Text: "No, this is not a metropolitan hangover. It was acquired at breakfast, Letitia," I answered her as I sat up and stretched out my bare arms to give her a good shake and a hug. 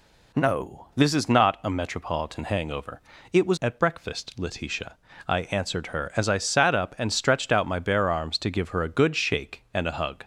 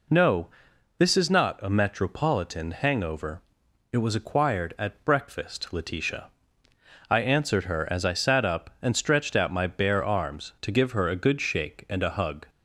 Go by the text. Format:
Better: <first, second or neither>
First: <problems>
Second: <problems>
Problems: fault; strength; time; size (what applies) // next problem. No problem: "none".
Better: second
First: skips "acquired"; at 3.5 s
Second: none